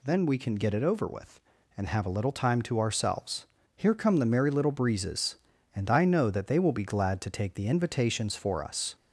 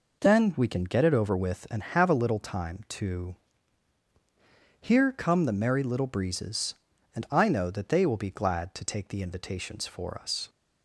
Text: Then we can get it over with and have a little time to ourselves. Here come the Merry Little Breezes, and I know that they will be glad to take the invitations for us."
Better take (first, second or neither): first